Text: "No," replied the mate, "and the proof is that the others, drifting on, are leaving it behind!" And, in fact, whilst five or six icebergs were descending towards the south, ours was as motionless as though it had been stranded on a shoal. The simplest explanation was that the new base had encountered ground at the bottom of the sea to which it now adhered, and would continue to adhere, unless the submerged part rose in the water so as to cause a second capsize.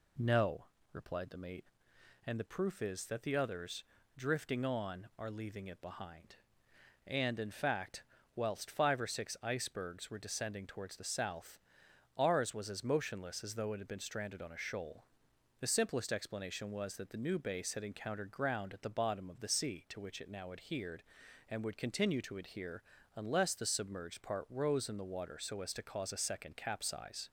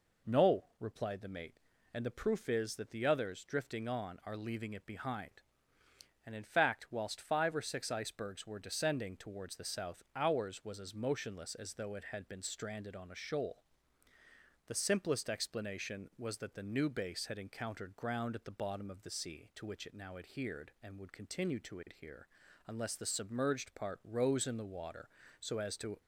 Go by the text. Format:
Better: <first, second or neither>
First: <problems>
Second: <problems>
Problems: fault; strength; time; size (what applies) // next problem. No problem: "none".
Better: first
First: none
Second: stops before "cause a second capsize"; at 26.0 s